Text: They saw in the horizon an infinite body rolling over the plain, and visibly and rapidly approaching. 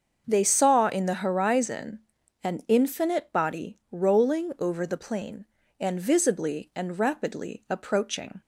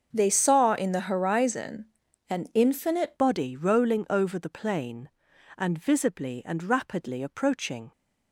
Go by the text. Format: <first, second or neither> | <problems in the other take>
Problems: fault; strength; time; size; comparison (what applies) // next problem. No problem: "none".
first | starts louder than the rest; until 1.1 s; 6.5 dB; also in the first // pauses between "horizon" and "an"; at 1.8 s; 0.44 s long; also in the first // changes voice at "body"; from 3.1 s on; 4.8 s long